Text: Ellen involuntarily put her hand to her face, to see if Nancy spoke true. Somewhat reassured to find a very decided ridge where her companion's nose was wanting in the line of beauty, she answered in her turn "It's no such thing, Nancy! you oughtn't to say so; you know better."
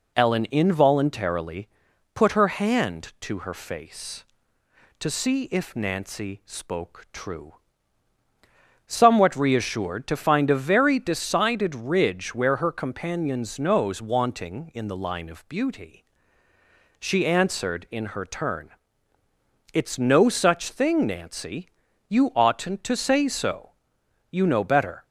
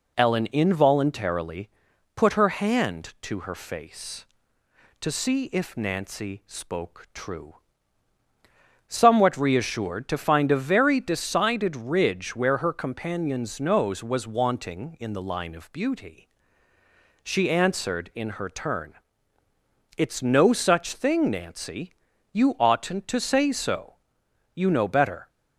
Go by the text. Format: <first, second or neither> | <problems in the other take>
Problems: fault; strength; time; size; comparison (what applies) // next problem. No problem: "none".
second | pauses between "involuntarily" and "put"; noticeable; at 1.6 s; 0.46 s long; noticeable in the second // skips "was"; at 14.0 s // pauses between "turn" and "It's"; at 18.7 s; 1.0 s long; also in the second